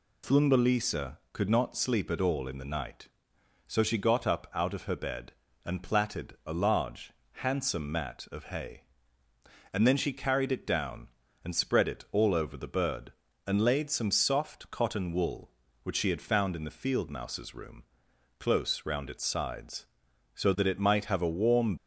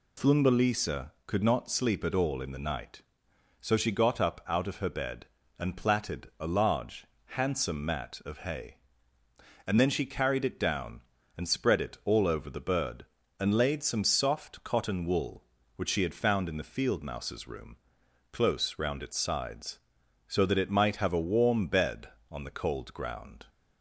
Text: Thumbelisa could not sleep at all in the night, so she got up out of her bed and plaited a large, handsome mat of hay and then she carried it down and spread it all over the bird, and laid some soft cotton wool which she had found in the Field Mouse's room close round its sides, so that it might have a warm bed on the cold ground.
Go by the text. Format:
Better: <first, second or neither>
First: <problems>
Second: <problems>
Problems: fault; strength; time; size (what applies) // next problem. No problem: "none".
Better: second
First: pauses between "room" and "close"; noticeable; at 17.8 s; 0.56 s long // stops before "bed on the cold ground"; at 21.7 s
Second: pauses between "room" and "close"; noticeable; at 17.7 s; 0.56 s long